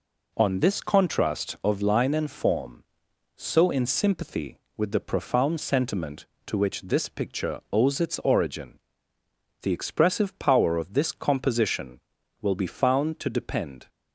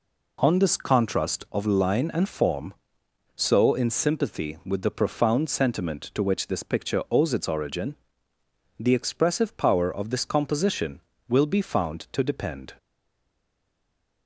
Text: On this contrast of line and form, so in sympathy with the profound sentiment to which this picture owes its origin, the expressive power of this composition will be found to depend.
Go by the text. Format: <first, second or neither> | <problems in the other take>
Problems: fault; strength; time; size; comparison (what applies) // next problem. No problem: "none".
first | stays silent after the last word; noticeable; from 12.7 s on; 1.5 s long